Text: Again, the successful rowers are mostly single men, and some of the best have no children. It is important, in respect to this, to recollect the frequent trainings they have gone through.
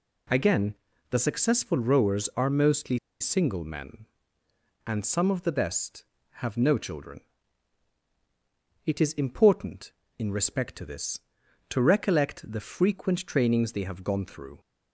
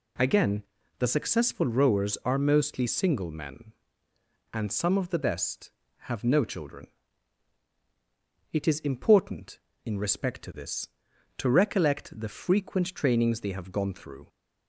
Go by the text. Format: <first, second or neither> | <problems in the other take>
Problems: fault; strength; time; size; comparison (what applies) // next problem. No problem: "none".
second | pauses between "mostly" and "single"; slight; at 2.9 s; 0.22 s long